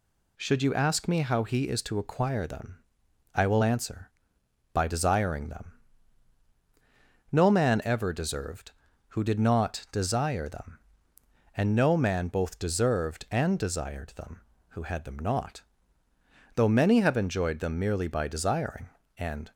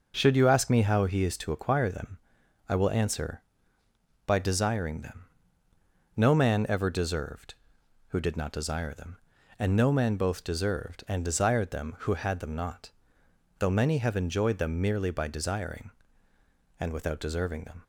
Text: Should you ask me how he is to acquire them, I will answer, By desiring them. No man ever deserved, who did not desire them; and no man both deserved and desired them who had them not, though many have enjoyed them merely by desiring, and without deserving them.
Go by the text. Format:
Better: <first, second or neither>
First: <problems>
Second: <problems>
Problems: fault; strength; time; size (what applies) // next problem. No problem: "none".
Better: second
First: stops before "without deserving them"; at 19.5 s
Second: none